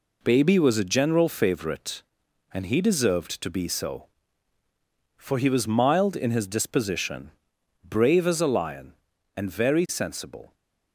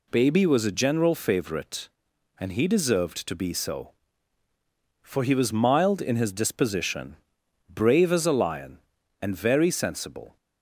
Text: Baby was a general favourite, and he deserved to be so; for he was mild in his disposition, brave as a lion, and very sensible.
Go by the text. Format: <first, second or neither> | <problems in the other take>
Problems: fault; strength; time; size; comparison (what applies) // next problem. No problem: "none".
second | gets quieter; noticeable; throughout; 6 dB